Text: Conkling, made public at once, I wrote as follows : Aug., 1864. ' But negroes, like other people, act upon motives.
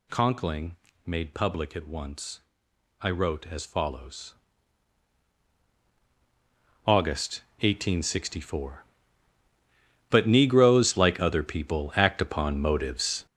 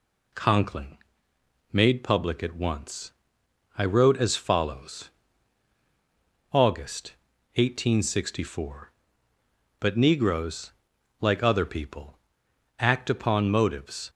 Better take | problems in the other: second | gets louder; noticeable; throughout; 4.5 dB

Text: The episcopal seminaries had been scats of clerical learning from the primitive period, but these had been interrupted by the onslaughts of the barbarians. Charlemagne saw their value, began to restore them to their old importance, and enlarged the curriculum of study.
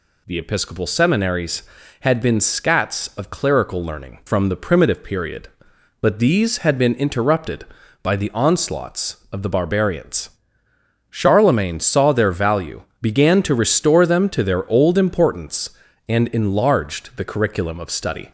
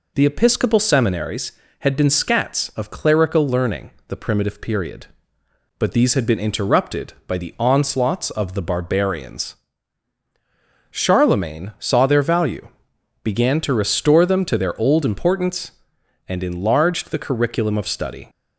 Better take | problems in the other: first | skips "from"; at 3.9 s

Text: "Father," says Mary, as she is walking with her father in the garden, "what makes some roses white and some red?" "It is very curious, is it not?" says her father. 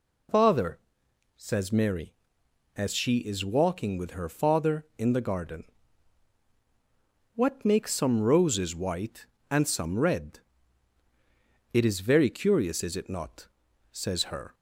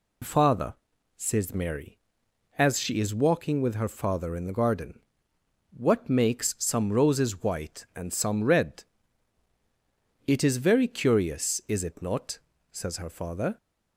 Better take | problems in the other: second | stops before "father"; at 14.5 s

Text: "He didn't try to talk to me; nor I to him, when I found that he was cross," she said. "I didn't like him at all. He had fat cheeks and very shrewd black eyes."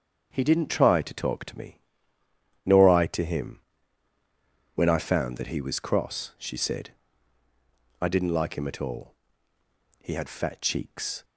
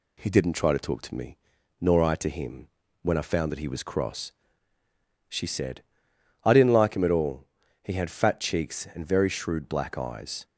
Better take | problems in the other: second | starts louder than the rest; until 1.3 s; 7 dB // stops before "and very shrewd black eyes"; at 11.2 s

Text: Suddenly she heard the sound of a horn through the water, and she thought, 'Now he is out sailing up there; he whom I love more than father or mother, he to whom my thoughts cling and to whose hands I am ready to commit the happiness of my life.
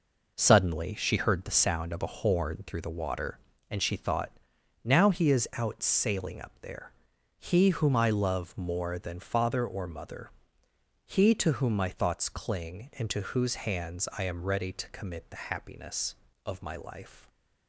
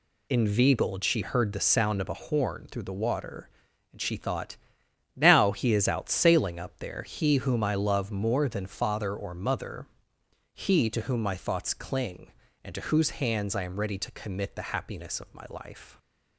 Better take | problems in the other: first | says "Inveigled" for "Suddenly"; at 0.2 s

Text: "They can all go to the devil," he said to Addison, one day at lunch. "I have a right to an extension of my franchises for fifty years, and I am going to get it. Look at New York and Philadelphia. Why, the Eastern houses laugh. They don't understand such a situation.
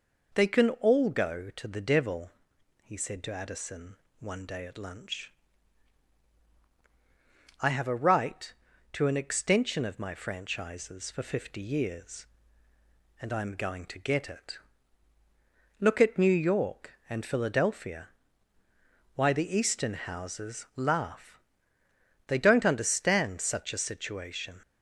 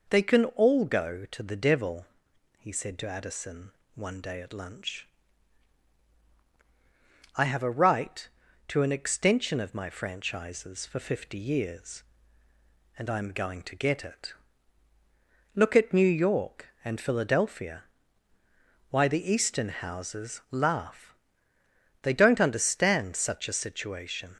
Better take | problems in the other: neither | none

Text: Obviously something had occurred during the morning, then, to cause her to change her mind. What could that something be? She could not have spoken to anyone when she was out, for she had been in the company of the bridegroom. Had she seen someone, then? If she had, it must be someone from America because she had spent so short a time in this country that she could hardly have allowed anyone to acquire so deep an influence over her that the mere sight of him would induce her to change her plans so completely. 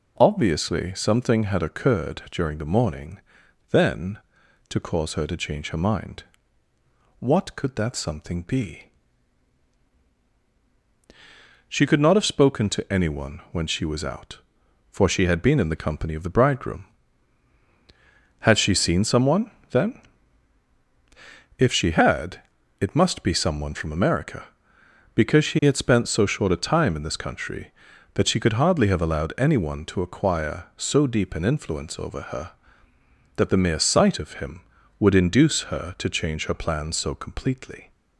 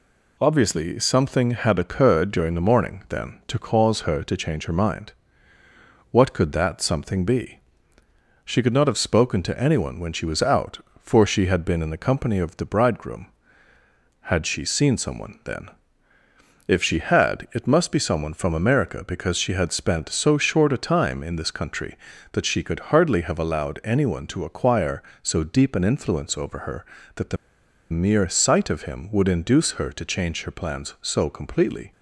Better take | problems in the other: first | pauses between "the" and "mere"; noticeable; at 27.3 s; 0.55 s long

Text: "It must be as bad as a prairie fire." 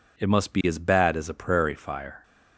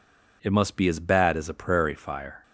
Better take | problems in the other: neither | none

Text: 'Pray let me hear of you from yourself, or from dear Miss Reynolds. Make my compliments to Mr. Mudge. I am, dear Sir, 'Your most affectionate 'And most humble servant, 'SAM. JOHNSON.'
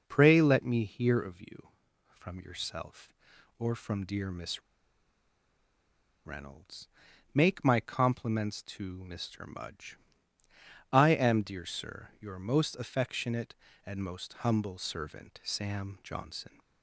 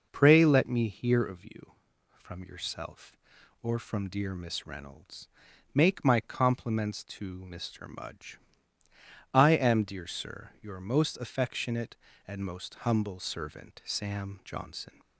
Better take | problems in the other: second | pauses between "Miss" and "Reynolds"; strong; at 4.6 s; 1.6 s long

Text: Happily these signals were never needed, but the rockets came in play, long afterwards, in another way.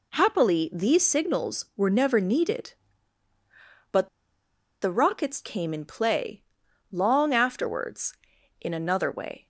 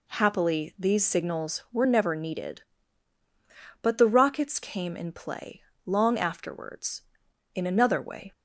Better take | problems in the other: second | pauses between "but" and "the"; noticeable; at 4.0 s; 0.74 s long

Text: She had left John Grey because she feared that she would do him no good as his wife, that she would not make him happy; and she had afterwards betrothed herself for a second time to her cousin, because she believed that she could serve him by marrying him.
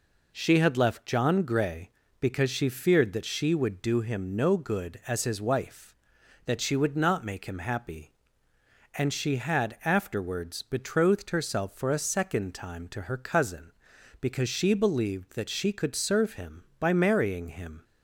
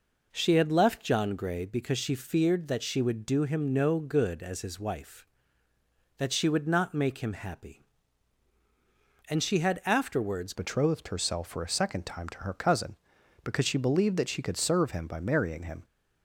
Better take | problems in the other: first | changes voice at "betrothed"; from 10.5 s on; 5.3 s long

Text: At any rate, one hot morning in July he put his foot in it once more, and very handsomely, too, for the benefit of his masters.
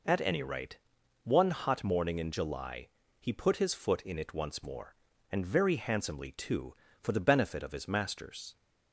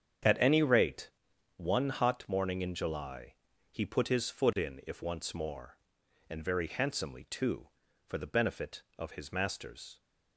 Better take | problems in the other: first | starts louder than the rest; strong; until 1.7 s; 8 dB // pauses between "July" and "he"; slight; at 3.3 s; 0.36 s long; slight in the first // says "if" for "it"; at 4.8 s

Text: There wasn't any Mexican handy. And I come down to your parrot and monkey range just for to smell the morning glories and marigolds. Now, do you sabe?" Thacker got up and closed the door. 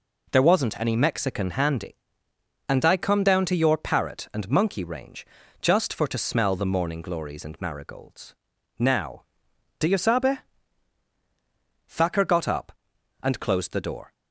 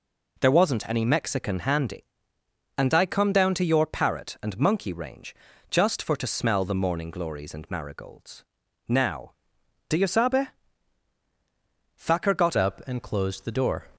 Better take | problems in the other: first | pauses between "range" and "just"; slight; at 5.3 s; 0.36 s long; slight in the first // changes voice at "up"; from 12.5 s on; 1.3 s long

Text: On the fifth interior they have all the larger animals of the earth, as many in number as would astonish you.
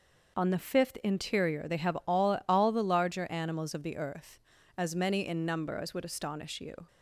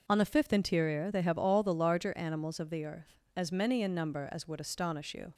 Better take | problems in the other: second | says "all" twice; at 2.4 s

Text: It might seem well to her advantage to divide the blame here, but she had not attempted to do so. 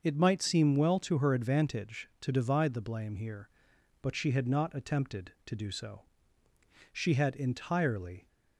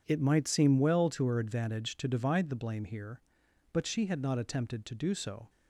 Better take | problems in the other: second | starts louder than the rest; until 1.0 s; 6 dB // goes on to say "She had entirely"; from 6.9 s on; 1.3 s long

